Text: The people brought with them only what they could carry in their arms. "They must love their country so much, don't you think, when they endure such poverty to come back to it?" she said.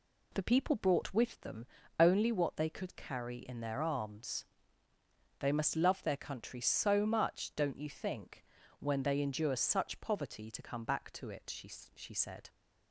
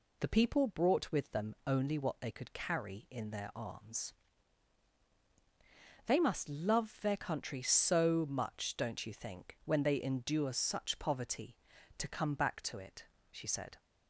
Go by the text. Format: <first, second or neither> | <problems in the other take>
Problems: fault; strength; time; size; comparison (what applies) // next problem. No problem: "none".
second | pauses between "them" and "only"; slight; at 1.6 s; 0.32 s long // says "she" twice; at 11.9 s